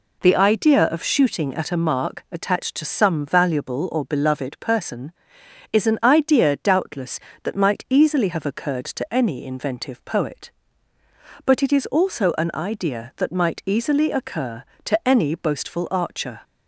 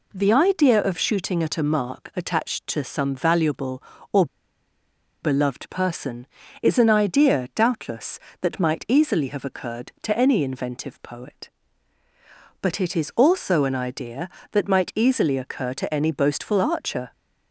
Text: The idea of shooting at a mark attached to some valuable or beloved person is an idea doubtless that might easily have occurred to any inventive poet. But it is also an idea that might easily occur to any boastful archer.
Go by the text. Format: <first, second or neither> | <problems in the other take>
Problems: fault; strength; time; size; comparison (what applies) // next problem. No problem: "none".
first | pauses between "or" and "beloved"; noticeable; at 4.2 s; 0.97 s long